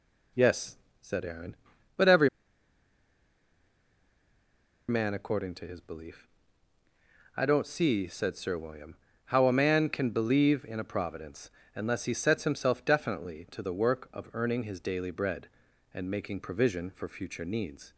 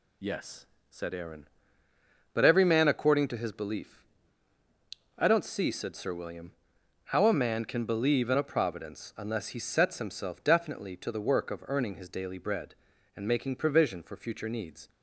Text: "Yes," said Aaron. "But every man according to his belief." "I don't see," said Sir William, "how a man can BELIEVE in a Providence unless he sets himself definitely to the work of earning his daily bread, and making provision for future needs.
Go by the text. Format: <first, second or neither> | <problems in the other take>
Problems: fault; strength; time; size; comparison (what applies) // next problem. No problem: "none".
second | pauses between "every" and "man"; strong; at 2.2 s; 2.6 s long // pauses between "Providence" and "unless"; slight; at 11.4 s; 0.26 s long